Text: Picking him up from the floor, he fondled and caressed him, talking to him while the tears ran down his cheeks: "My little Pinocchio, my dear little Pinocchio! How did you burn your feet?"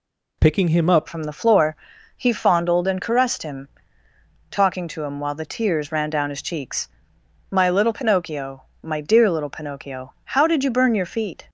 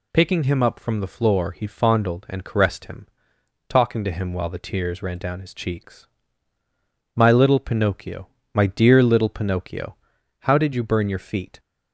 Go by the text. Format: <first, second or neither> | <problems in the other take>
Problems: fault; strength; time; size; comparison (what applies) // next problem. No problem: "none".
second | changes voice at "from"; from 1.0 s on; 10.4 s long